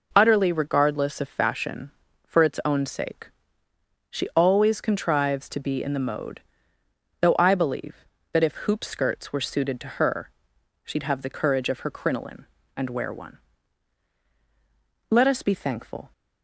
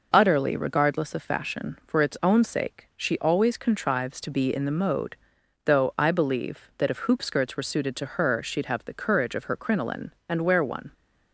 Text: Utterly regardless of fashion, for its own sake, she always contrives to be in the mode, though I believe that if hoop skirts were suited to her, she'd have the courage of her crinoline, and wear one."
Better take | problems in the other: second | goes on to say "Let us be thankful"; noticeable; from 15.0 s on; 1.0 s long

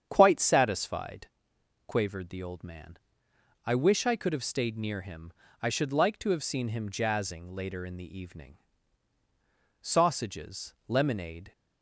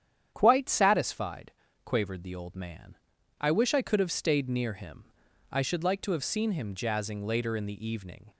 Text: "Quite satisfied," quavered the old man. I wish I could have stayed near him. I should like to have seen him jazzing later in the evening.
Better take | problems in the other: second | starts louder than the rest; strong; until 1.1 s; 8 dB; strong in the second // goes on to say "Sausages lemonade"; strong; from 9.8 s on; 1.7 s long

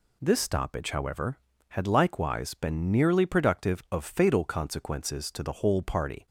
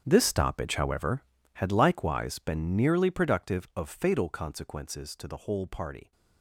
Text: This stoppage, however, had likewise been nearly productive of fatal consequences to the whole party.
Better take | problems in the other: first | gets quieter; strong; throughout; 15.5 dB

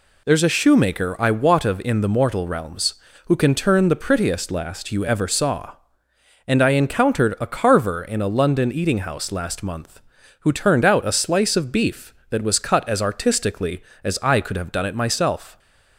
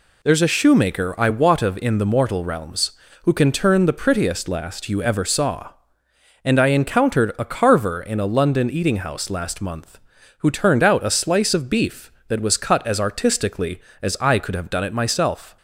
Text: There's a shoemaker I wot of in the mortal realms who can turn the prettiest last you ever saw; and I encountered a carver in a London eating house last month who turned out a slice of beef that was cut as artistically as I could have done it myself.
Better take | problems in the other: neither | none

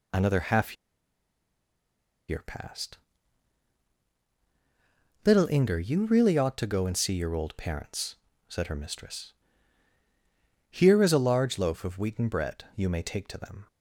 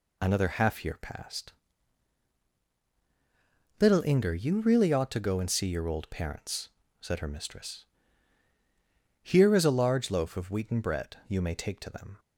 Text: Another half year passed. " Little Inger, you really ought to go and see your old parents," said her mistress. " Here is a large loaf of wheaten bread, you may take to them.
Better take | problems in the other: second | pauses between "half" and "year"; strong; at 0.7 s; 1.5 s long

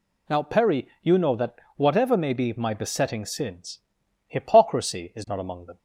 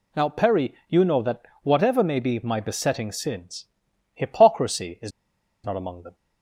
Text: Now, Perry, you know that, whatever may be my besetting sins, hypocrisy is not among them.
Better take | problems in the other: first | pauses between "is" and "not"; noticeable; at 5.1 s; 0.53 s long

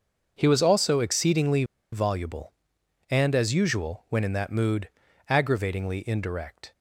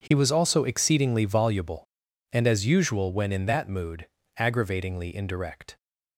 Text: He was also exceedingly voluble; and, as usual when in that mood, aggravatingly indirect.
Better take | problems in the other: second | starts louder than the rest; until 1.3 s; 6.5 dB // pauses between "exceedingly" and "voluble"; slight; at 1.6 s; 0.28 s long

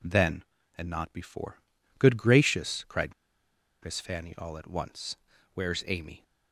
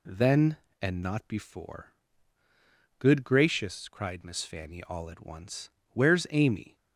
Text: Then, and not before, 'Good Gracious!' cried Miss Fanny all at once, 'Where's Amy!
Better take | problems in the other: second | pauses between "cried" and "Miss"; noticeable; at 3.1 s; 0.69 s long

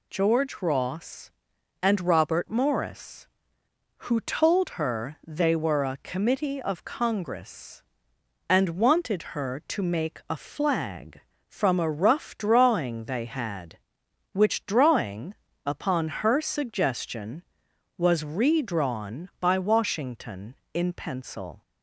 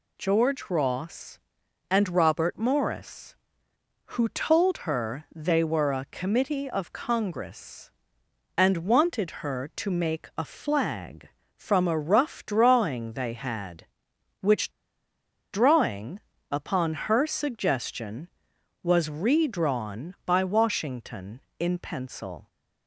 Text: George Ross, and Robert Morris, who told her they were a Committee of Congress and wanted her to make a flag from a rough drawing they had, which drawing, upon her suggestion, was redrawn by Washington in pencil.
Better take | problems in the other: first | pauses between "which" and "drawing"; noticeable; at 14.7 s; 0.81 s long

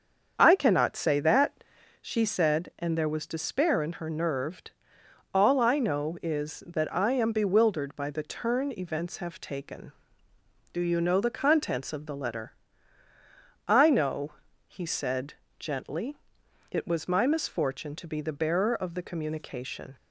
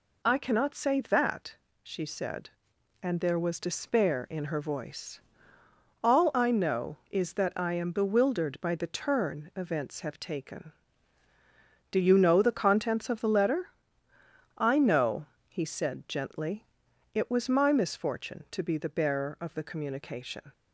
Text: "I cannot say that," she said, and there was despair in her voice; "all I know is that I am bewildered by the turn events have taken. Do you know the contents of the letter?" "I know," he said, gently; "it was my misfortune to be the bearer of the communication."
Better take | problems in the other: second | starts louder than the rest; until 1.3 s; 7 dB // says "nerved" for "voice"; at 4.1 s

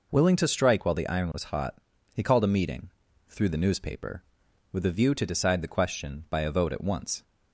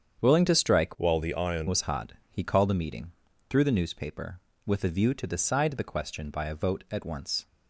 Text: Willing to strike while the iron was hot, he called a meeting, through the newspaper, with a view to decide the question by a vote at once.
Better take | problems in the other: first | starts louder than the rest; strong; until 1.2 s; 7.5 dB // changes voice from "while" to "iron"; from 0.9 to 1.6 s; 0.7 s long

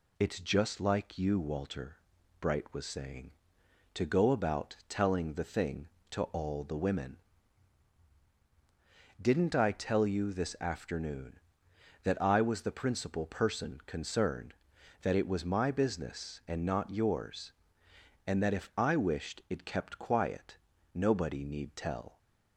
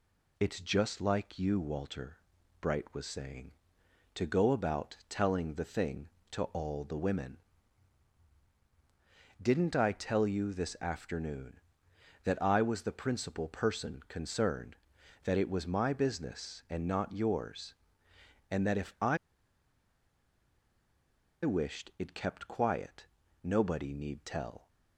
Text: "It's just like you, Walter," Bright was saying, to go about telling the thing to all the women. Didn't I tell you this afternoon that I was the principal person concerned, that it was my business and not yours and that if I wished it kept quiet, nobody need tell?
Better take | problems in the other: first | pauses between "I" and "wished"; strong; at 19.1 s; 2.2 s long

